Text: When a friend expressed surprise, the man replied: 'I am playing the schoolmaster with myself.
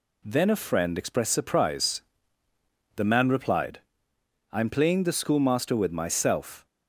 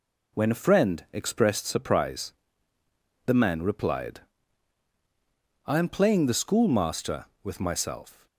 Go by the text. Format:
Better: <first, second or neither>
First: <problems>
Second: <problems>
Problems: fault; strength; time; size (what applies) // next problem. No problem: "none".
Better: second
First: says "Then" for "When"; at 0.2 s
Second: none